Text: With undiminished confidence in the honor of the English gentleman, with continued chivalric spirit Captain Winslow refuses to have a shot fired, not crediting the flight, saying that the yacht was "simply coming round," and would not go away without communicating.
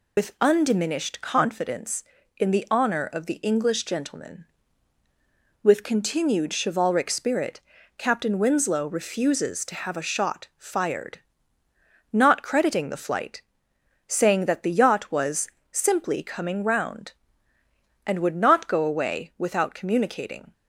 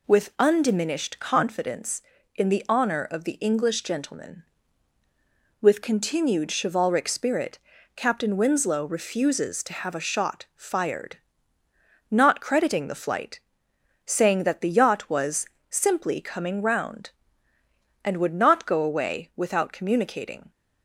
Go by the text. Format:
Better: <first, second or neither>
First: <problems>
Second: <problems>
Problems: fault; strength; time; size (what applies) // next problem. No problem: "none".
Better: second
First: loses the start of "With"; at 0.1 s; 90 ms // pauses between "spirit" and "Captain"; at 7.6 s; 0.38 s long // pauses between "was" and "simply"; slight; at 15.4 s; 0.24 s long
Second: pauses between "spirit" and "Captain"; at 7.5 s; 0.38 s long // pauses between "was" and "simply"; slight; at 15.4 s; 0.24 s long